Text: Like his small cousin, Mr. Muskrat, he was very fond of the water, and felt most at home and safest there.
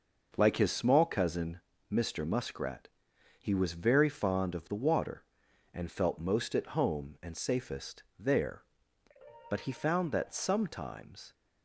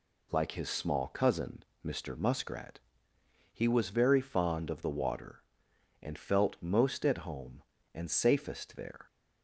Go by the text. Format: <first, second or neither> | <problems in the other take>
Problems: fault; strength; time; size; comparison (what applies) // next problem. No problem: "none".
second | pauses between "safest" and "there"; slight; at 8.0 s; 0.16 s long // goes on to say "But he found that sometimes"; strong; from 9.5 s on; 1.8 s long